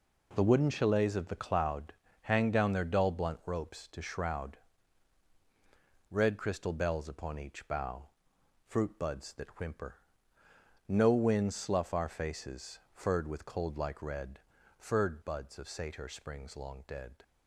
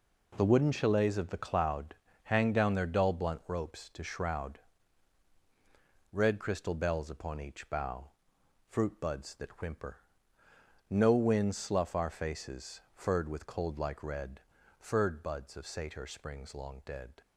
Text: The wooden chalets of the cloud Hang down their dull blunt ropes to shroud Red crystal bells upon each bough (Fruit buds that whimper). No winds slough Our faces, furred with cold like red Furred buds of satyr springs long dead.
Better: neither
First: pauses between "cloud" and "Hang"; slight; at 1.9 s; 0.30 s long // pauses between "shroud" and "Red"; strong; at 4.5 s; 1.5 s long // pauses between "red" and "Furred"; at 14.3 s; 0.38 s long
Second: pauses between "cloud" and "Hang"; slight; at 1.9 s; 0.30 s long // pauses between "shroud" and "Red"; strong; at 4.5 s; 1.5 s long // pauses between "red" and "Furred"; at 14.4 s; 0.38 s long

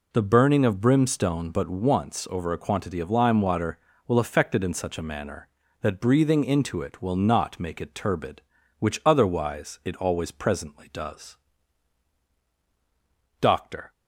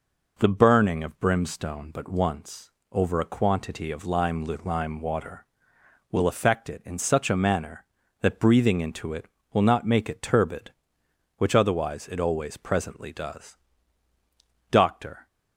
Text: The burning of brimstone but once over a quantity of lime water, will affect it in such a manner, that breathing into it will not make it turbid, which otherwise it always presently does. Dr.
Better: first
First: none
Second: pauses between "once" and "over"; slight; at 2.7 s; 0.22 s long // says "lime" twice; at 4.4 s

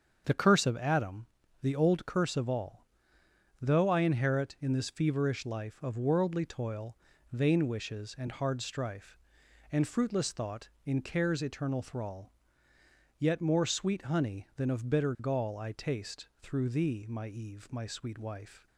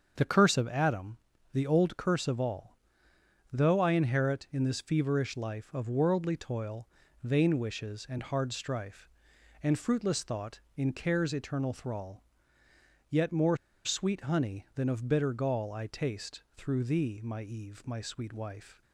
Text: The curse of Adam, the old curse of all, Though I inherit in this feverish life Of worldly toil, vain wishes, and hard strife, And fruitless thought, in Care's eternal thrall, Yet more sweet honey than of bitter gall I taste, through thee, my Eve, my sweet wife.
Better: first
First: starts louder than the rest; until 1.2 s; 7 dB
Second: starts louder than the rest; until 1.1 s; 7 dB // pauses between "more" and "sweet"; slight; at 13.5 s; 0.27 s long

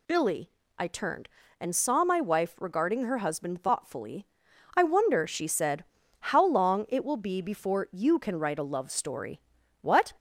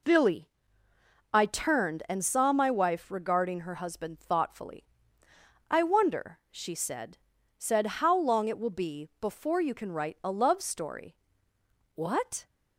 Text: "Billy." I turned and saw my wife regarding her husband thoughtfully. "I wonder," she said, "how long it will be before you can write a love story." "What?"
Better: first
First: none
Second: says "said" twice; at 7.5 s

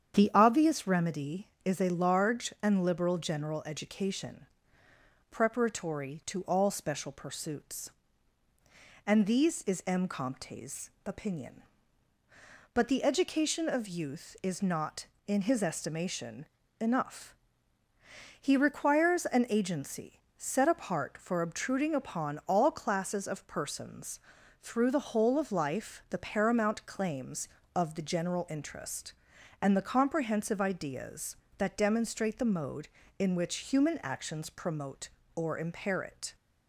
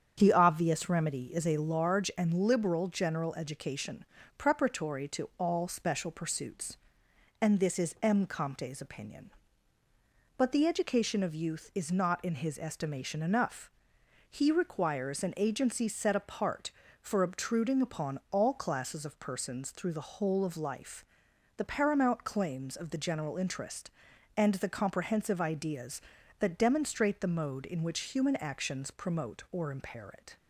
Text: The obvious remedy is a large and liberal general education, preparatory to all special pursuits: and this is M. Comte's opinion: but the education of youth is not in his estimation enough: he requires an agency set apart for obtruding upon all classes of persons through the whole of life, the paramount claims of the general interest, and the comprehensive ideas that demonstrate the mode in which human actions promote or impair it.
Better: second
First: starts louder than the rest; strong; until 1.1 s; 8.5 dB // says "these" for "this"; at 9.2 s // pauses between "Comte's" and "opinion"; slight; at 10.8 s; 0.16 s long // pauses between "estimation" and "enough"; slight; at 16.4 s; 0.34 s long // pauses between "agency" and "set"; slight; at 20.2 s; 0.16 s long // pauses between "persons" and "through"; at 24.2 s; 0.40 s long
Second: starts louder than the rest; strong; until 1.1 s; 7.5 dB

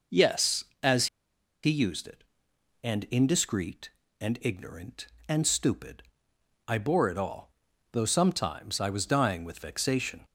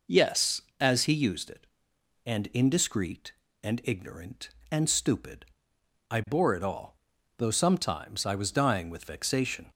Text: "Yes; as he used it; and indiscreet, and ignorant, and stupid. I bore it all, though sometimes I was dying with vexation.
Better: second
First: pauses between "as" and "he"; noticeable; at 1.0 s; 0.57 s long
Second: none

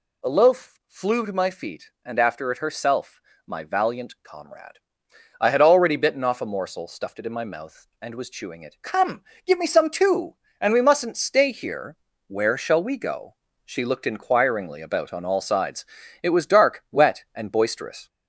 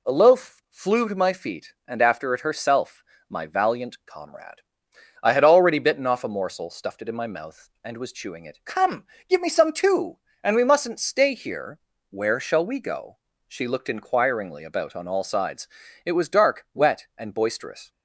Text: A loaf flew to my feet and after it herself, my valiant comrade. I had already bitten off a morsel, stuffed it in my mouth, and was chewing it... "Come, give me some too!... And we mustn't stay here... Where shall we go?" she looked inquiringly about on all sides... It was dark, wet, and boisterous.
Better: second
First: gets louder; slight; throughout; 3 dB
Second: none

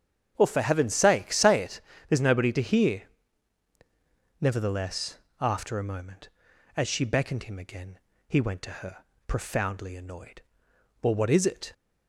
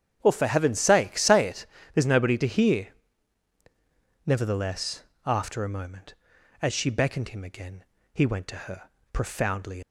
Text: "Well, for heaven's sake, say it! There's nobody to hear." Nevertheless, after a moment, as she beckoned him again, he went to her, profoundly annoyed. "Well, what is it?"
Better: first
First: starts louder than the rest; strong; until 1.3 s; 8 dB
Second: starts louder than the rest; strong; until 1.2 s; 8.5 dB // stops before "annoyed Well what is it"; at 9.8 s

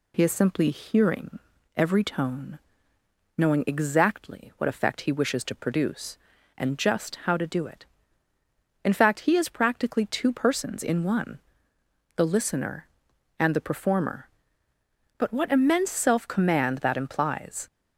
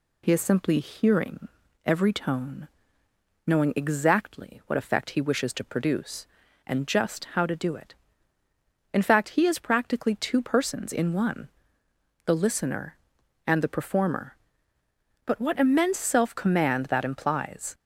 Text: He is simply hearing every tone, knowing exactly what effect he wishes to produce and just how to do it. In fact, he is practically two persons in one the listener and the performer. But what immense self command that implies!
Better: neither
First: pauses between "hearing" and "every"; slight; at 1.3 s; 0.36 s long // pauses between "one" and "the"; noticeable; at 11.4 s; 0.74 s long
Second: pauses between "hearing" and "every"; slight; at 1.4 s; 0.36 s long // pauses between "one" and "the"; noticeable; at 11.4 s; 0.74 s long

